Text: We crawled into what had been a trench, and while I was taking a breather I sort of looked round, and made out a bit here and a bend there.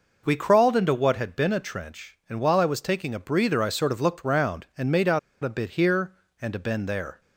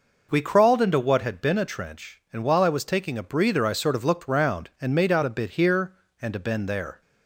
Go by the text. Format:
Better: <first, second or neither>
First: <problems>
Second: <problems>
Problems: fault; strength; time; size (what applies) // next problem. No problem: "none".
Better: second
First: pauses between "out" and "a"; slight; at 5.1 s; 0.24 s long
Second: none